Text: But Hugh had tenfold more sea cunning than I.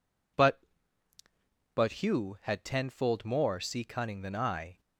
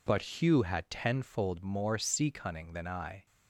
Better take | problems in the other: second | says "But" twice; at 1.7 s

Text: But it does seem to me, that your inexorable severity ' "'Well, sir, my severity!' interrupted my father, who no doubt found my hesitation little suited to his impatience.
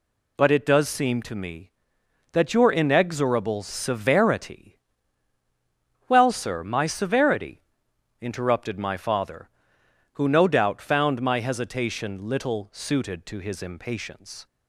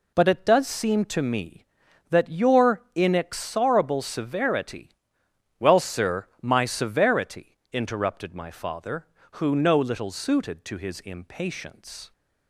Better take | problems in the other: first | skips "doubt found my hesitation"; at 9.7 s

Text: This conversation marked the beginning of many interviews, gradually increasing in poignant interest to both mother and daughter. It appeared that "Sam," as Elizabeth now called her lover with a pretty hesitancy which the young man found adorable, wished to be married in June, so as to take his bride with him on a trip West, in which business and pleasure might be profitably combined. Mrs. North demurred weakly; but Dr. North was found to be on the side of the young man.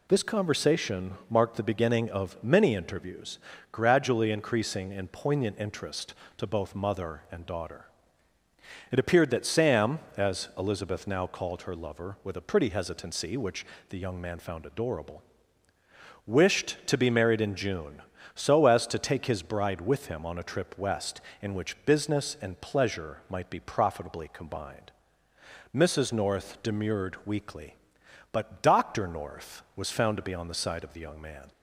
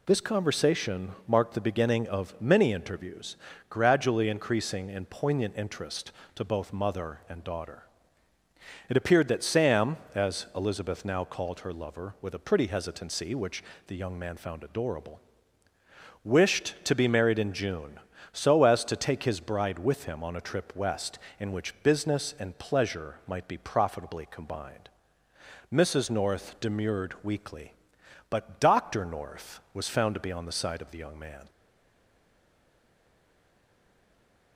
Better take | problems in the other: first | pauses between "which" and "the"; slight; at 13.6 s; 0.24 s long; slight in the first // stays silent after the last word; strong; from 31.4 s on; 3.1 s long

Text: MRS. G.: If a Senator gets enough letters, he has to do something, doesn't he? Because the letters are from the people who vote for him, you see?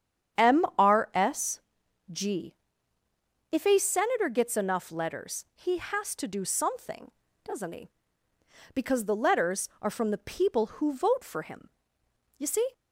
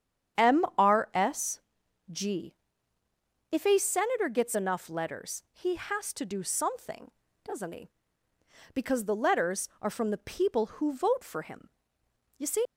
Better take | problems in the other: first | starts louder than the rest; strong; until 1.5 s; 8.5 dB; strong in the first // leaves "see" unfinished; at 12.6 s; 70 ms

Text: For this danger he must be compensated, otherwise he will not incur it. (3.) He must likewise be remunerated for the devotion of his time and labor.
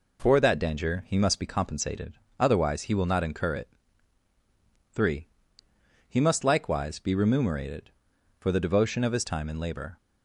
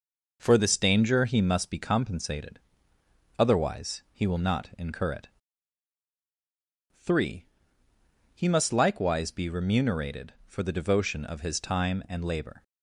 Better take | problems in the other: second | says "that" for "this"; at 0.3 s

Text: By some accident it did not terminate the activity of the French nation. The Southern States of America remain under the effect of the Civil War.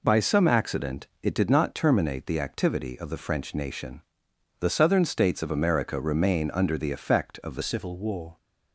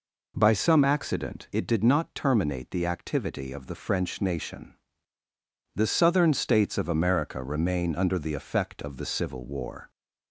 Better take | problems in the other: second | pauses between "accident" and "it"; slight; at 1.0 s; 0.16 s long // changes voice at "Civil"; from 7.6 s on; 0.7 s long

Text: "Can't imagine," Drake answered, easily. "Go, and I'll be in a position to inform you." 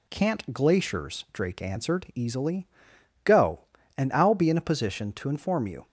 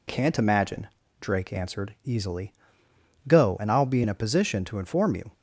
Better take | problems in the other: second | says "glaciers" for "imagine"; at 0.5 s

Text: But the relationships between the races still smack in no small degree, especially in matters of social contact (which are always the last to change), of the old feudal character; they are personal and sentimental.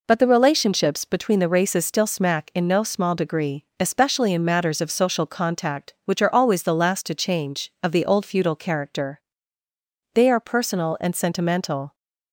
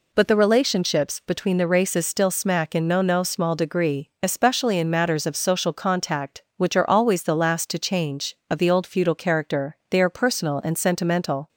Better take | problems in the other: first | says "no" twice; at 3.0 s

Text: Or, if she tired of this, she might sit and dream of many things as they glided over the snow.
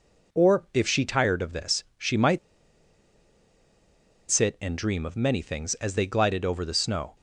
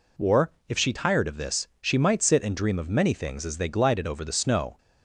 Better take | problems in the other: second | pauses between "might" and "sit"; strong; at 2.3 s; 1.8 s long

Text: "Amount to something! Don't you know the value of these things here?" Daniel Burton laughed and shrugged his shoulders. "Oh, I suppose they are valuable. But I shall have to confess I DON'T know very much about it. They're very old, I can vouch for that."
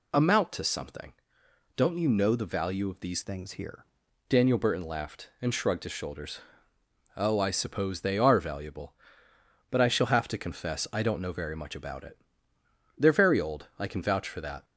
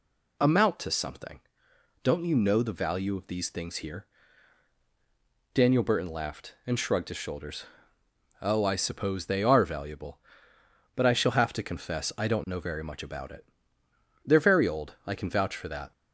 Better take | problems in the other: second | changes voice from "things" to "here"; from 3.2 to 3.8 s; 0.6 s long

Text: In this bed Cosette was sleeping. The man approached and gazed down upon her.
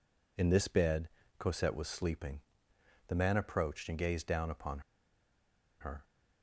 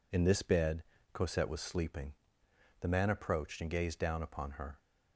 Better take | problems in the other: second | pauses between "bed" and "Cosette"; slight; at 1.0 s; 0.28 s long; slight in the second // pauses between "upon" and "her"; at 4.7 s; 1.0 s long

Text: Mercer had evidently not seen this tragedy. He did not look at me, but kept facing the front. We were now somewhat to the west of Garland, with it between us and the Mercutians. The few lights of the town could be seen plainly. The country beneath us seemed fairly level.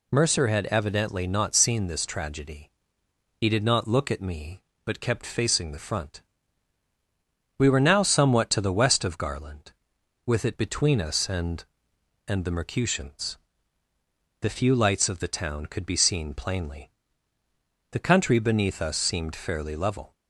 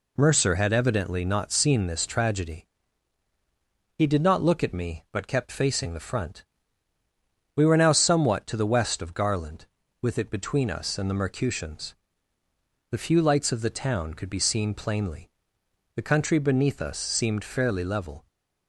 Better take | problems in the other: second | says "and" twice; at 12.2 s

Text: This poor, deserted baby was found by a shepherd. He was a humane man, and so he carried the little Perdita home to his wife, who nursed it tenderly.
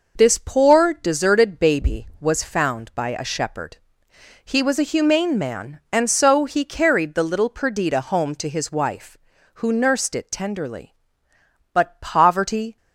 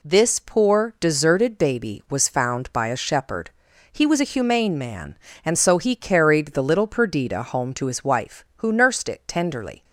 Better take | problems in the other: second | goes on to say "But poverty"; noticeable; from 11.7 s on; 1.0 s long

